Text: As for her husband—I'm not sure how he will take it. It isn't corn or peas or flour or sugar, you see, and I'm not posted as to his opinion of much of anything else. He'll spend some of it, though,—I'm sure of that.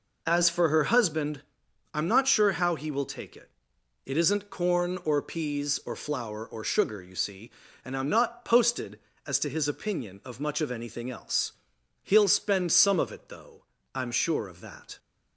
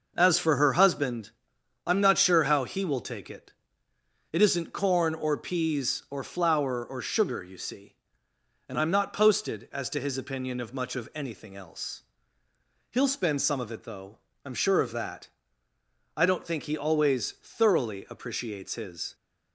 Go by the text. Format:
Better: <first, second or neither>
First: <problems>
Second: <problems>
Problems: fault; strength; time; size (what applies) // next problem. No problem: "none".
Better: first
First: none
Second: goes on to say "I don't think he always thoroughly appreciates his"; strong; from 16.1 s on; 2.9 s long